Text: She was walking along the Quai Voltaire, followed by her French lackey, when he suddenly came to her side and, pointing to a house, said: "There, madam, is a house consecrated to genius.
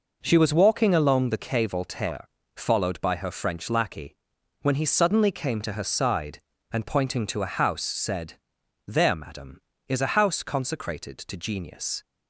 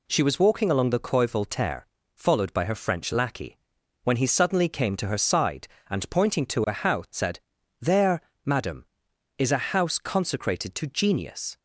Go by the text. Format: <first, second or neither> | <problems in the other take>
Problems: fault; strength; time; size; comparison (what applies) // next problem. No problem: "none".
neither | none